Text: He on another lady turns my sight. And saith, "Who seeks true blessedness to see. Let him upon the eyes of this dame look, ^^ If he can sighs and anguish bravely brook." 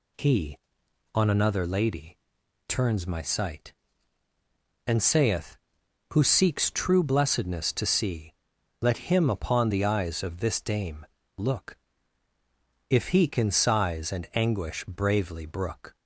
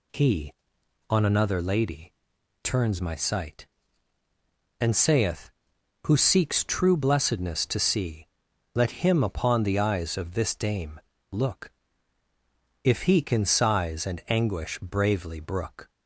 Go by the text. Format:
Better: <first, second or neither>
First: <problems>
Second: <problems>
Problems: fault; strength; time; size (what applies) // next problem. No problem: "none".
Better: neither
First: pauses between "lady" and "turns"; noticeable; at 2.1 s; 0.50 s long // pauses between "dame" and "look"; slight; at 11.0 s; 0.32 s long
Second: pauses between "lady" and "turns"; noticeable; at 2.1 s; 0.50 s long // pauses between "dame" and "look"; slight; at 10.9 s; 0.32 s long